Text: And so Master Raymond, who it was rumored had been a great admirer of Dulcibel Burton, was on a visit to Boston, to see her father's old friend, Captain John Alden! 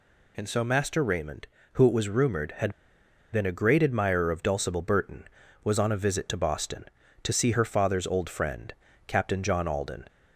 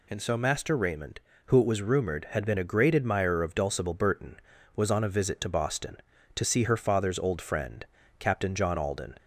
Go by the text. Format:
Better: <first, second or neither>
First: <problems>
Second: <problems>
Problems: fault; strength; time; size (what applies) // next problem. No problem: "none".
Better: second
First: pauses between "had" and "been"; noticeable; at 2.7 s; 0.60 s long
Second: none